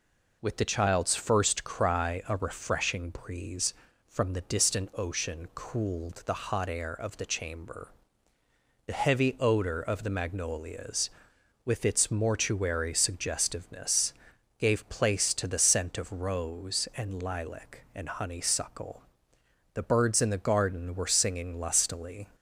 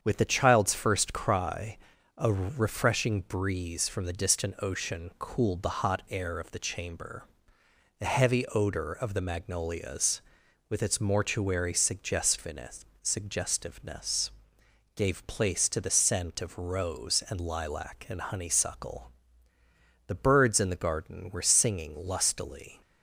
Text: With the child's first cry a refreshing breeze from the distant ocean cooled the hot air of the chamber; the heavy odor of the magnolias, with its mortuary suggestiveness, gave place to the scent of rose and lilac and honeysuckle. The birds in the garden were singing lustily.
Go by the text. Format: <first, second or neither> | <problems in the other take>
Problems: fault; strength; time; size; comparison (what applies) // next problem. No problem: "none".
first | starts louder than the rest; strong; until 1.0 s; 7.5 dB // pauses between "cry" and "a"; at 1.7 s; 0.40 s long // says "suggestiveness" twice; at 13.0 s